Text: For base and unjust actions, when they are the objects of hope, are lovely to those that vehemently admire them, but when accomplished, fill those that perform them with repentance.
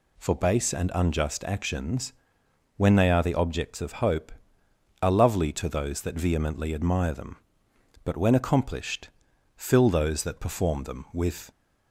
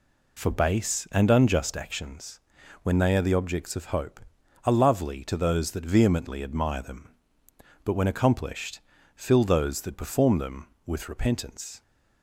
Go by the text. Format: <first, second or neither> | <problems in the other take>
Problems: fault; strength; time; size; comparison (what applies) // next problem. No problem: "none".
second | stops before "repentance"; at 11.5 s